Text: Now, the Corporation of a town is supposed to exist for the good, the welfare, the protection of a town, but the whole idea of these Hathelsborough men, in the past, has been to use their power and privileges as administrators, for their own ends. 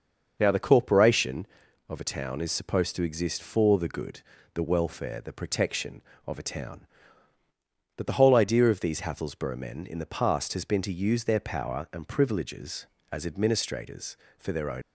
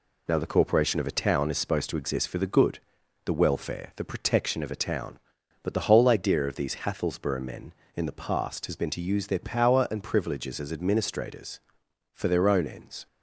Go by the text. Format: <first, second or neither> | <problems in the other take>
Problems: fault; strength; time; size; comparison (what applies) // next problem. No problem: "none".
second | starts louder than the rest; until 1.4 s; 6 dB // stops before "ends"; at 14.8 s